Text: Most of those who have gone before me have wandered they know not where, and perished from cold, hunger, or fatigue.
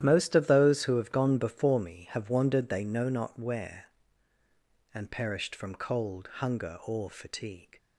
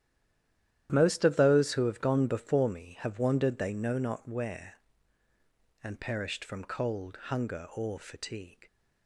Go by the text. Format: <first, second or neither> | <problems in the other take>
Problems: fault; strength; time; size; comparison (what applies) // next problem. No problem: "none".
first | stays silent before the first word; slight; until 0.8 s; 0.8 s long // starts louder than the rest; strong; until 1.9 s; 11.5 dB; strong in the first